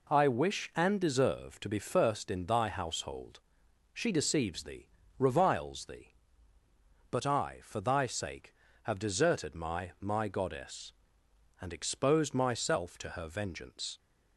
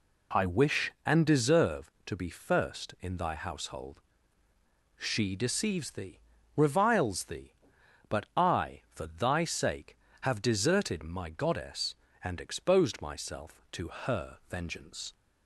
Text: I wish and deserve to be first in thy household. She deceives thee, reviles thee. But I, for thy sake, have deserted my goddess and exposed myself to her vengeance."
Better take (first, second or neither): second